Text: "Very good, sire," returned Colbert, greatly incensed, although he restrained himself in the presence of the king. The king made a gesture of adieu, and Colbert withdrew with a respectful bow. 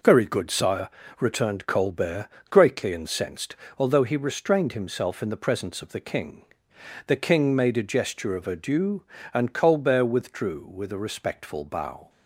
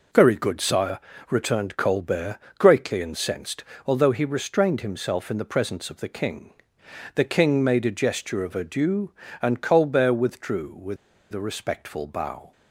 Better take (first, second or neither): first